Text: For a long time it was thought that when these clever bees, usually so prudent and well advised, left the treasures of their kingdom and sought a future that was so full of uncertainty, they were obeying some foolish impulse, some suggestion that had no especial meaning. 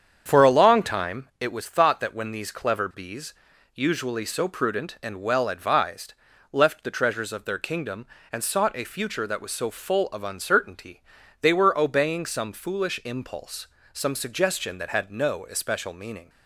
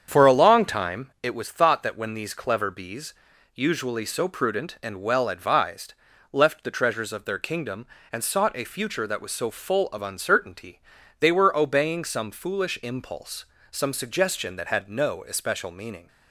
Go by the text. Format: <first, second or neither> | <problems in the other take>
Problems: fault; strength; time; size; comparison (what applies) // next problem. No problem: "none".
neither | starts louder than the rest; strong; the same in both